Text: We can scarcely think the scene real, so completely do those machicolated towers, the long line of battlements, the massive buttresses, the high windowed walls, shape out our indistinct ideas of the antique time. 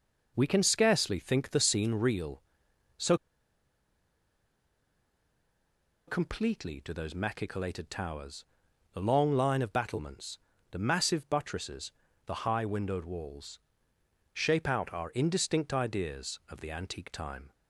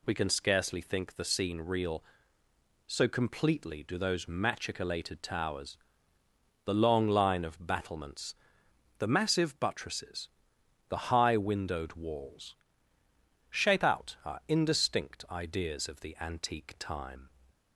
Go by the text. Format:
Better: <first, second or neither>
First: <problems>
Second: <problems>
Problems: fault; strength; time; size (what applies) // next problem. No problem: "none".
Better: second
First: pauses between "so" and "completely"; strong; at 3.1 s; 2.9 s long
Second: none